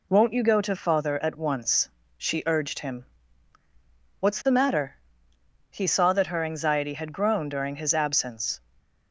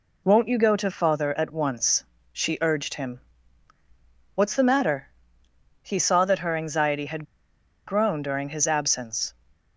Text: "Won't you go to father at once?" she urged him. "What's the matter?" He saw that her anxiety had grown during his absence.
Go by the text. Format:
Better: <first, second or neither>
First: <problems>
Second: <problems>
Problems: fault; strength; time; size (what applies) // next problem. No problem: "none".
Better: first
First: none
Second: pauses between "had" and "grown"; noticeable; at 7.2 s; 0.61 s long